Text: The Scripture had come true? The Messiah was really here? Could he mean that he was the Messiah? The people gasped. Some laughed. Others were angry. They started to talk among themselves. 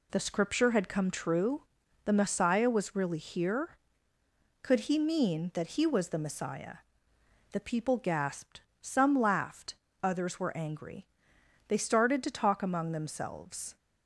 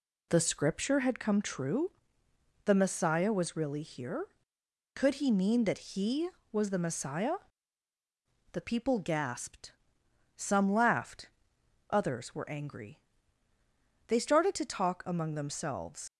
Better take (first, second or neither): first